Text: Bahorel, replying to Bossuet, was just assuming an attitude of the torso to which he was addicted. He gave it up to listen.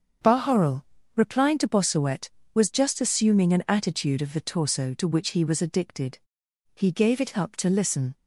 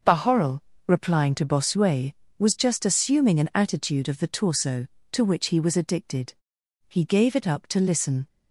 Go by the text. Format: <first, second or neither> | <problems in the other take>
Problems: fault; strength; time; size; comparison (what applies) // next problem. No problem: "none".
neither | starts louder than the rest; the same in both